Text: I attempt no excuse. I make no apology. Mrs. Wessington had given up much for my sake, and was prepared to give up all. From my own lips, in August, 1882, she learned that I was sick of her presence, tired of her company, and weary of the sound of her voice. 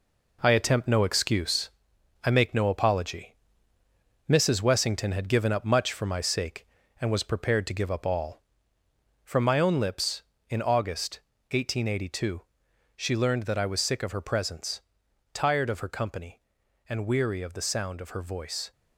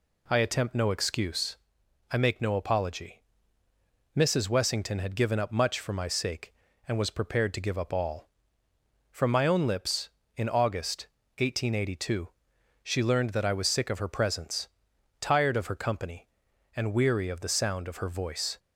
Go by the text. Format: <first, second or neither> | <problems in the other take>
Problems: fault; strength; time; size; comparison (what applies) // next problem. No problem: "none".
second | gets quieter; throughout; 6.5 dB